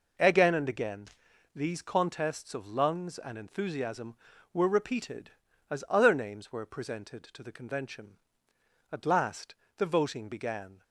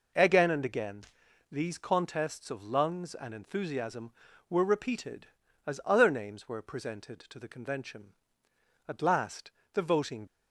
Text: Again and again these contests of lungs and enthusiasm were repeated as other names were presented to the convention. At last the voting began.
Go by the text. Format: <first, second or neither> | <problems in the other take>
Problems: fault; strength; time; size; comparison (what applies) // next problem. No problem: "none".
first | pauses between "again" and "these"; noticeable; at 1.0 s; 0.48 s long; noticeable in the first // pauses between "last" and "the"; slight; at 9.5 s; 0.22 s long; slight in the first // stops before "began"; at 10.2 s